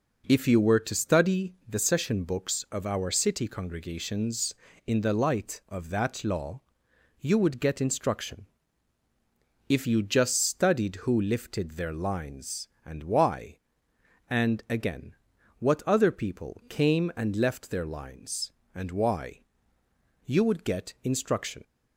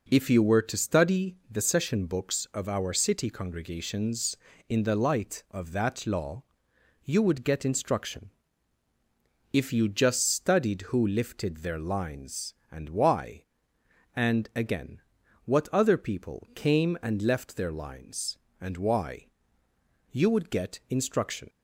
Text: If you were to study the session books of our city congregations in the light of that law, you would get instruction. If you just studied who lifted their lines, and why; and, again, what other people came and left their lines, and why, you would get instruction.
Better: neither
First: pauses between "study" and "the"; slight; at 1.5 s; 0.16 s long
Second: pauses between "study" and "the"; slight; at 1.3 s; 0.16 s long

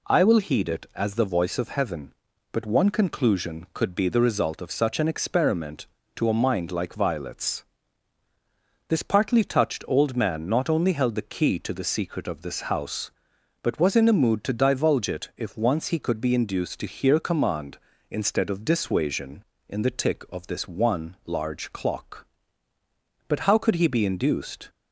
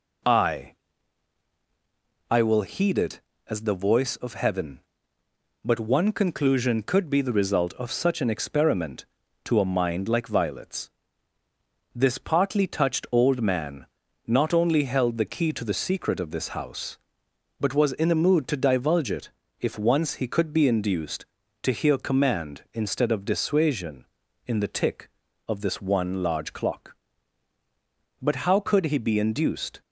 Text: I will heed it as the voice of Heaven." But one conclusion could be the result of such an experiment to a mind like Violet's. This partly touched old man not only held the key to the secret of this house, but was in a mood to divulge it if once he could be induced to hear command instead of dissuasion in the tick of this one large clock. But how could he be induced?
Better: first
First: none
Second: says "I" twice; at 2.3 s // pauses between "man" and "not"; at 13.8 s; 0.38 s long // pauses between "it" and "if"; slight; at 19.2 s; 0.32 s long

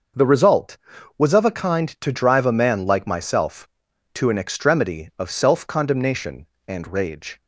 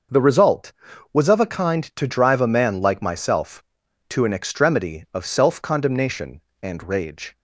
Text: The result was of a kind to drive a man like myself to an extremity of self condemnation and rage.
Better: neither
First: starts louder than the rest; noticeable; until 1.5 s; 6 dB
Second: starts louder than the rest; noticeable; until 1.5 s; 6 dB

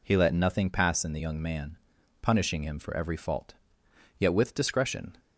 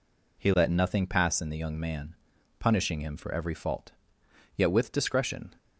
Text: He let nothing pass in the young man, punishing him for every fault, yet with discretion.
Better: neither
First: none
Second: none

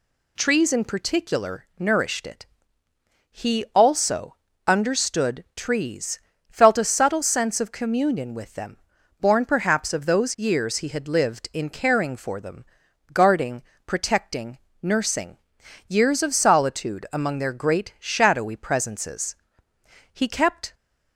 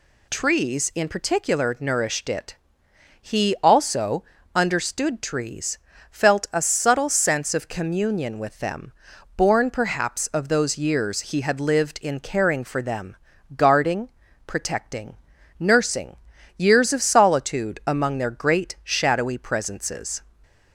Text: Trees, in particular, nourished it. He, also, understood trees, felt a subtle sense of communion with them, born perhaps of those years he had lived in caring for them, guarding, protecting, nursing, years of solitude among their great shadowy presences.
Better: second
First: goes on to say "He kept"; noticeable; from 20.1 s on; 0.62 s long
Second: none

